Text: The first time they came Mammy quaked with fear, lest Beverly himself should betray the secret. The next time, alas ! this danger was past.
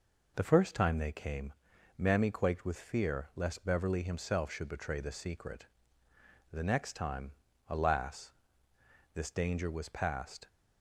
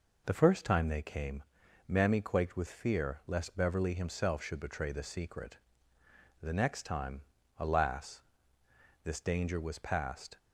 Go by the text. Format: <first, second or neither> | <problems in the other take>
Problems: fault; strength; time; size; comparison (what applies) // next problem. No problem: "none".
neither | pauses between "came" and "Mammy"; the same in both